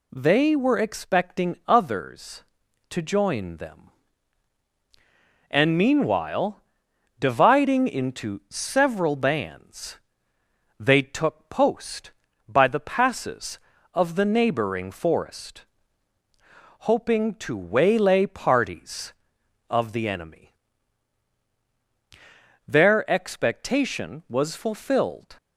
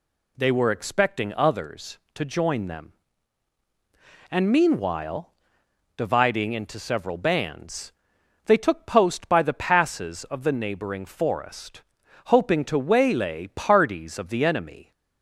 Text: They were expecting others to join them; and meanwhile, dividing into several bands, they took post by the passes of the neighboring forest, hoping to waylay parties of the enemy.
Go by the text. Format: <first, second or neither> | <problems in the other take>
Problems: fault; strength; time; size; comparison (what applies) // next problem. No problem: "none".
second | goes on to say "Their expectation was fulfilled"; strong; from 22.6 s on; 2.6 s long